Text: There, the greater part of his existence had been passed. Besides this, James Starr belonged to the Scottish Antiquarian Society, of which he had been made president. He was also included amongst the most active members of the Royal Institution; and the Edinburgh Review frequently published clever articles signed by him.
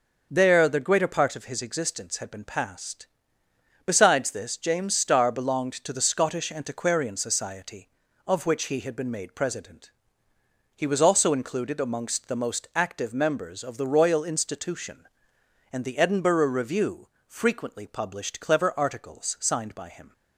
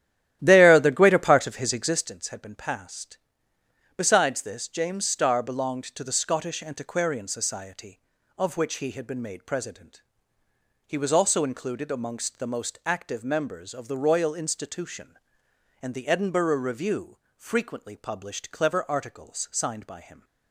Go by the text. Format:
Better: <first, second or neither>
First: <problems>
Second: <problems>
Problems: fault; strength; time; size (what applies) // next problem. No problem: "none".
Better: first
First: pauses between "Review" and "frequently"; slight; at 17.0 s; 0.20 s long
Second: starts louder than the rest; strong; until 2.1 s; 13 dB // pauses between "Review" and "frequently"; slight; at 17.1 s; 0.20 s long